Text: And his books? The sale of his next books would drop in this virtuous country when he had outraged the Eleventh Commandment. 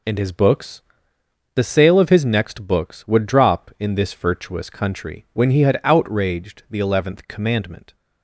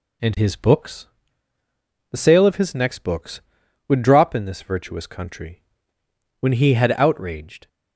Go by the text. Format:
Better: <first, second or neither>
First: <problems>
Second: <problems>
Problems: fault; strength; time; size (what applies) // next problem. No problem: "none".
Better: first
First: none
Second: pauses between "country" and "when"; noticeable; at 5.6 s; 0.76 s long // stops before "the Eleventh Commandment"; at 7.6 s